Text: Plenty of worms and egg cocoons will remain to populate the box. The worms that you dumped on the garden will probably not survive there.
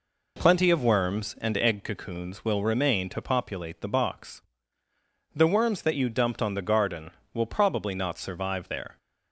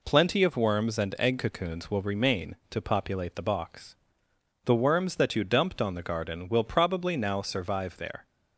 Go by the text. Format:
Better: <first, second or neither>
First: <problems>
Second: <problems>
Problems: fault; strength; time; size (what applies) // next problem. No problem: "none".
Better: first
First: none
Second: says "now" for "not"; at 7.1 s